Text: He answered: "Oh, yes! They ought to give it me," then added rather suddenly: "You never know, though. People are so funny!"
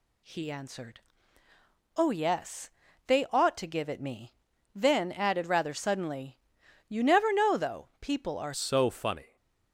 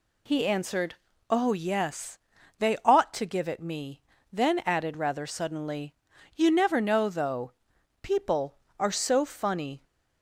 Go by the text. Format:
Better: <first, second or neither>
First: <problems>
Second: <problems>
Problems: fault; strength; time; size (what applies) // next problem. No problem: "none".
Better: second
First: changes voice at "so"; from 8.5 s on; 0.8 s long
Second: none